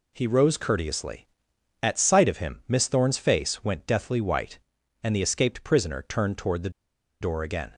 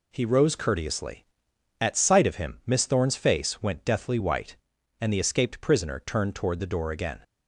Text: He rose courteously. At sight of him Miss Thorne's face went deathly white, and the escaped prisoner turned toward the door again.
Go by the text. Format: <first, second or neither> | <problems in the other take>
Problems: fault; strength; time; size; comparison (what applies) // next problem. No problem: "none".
second | pauses between "the" and "door"; noticeable; at 6.7 s; 0.50 s long